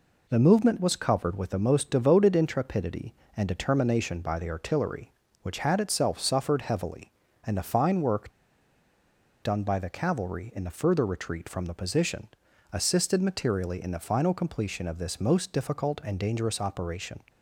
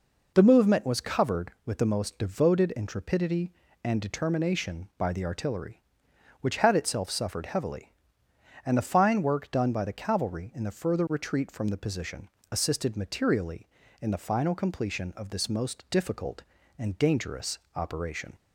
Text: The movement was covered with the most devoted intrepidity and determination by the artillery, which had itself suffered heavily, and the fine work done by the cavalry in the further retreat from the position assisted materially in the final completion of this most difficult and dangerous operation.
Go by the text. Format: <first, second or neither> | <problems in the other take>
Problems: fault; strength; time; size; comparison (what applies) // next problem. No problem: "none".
second | pauses between "work" and "done"; at 8.2 s; 1.1 s long // pauses between "position" and "assisted"; noticeable; at 12.2 s; 0.46 s long; slight in the second